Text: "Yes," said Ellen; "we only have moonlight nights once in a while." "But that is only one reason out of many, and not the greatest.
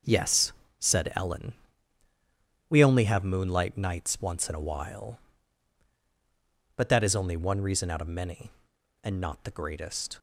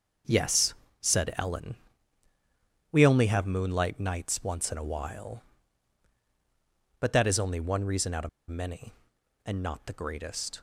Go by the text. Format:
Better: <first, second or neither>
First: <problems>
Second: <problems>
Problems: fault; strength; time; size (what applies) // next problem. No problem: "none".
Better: first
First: starts louder than the rest; until 1.3 s; 6 dB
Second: starts louder than the rest; until 1.5 s; 6 dB // pauses between "of" and "many"; slight; at 8.2 s; 0.20 s long